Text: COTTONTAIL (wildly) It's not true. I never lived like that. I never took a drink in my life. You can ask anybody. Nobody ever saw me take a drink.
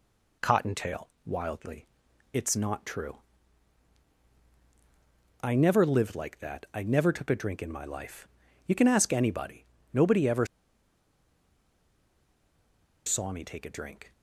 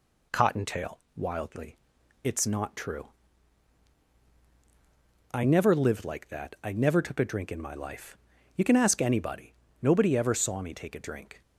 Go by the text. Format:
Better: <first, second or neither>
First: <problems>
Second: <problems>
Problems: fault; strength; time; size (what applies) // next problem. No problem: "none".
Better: second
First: pauses between "ever" and "saw"; strong; at 10.4 s; 2.5 s long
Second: none